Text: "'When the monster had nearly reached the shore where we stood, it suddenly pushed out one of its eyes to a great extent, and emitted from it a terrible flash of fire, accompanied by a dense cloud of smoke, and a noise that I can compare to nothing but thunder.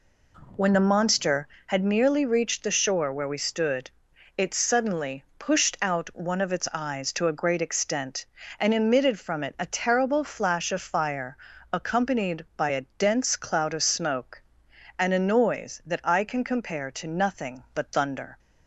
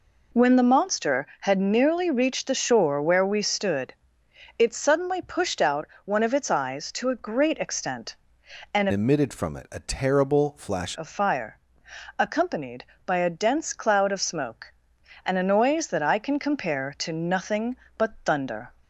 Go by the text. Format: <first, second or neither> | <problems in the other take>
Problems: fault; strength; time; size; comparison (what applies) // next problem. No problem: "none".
first | pauses between "out" and "one"; slight; at 5.8 s; 0.20 s long // changes voice from "emitted" to "flash"; from 8.9 to 10.9 s; 2.0 s long